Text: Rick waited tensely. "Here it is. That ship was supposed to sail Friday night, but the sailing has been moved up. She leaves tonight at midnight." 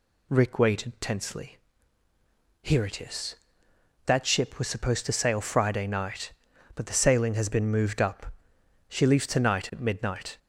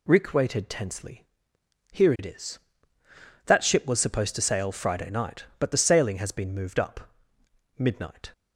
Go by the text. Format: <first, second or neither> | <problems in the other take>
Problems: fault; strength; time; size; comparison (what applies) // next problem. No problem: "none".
first | skips "She leaves tonight at"; at 7.4 s